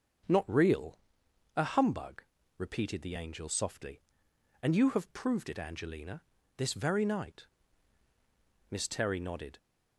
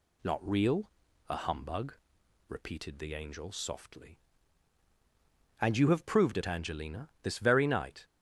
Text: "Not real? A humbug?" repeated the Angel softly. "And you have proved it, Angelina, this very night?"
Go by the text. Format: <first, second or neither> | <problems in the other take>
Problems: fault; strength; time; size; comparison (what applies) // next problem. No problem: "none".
second | starts louder than the rest; until 1.8 s; 7 dB // goes on to say "Miss Terry nodded"; noticeable; from 8.6 s on; 0.88 s long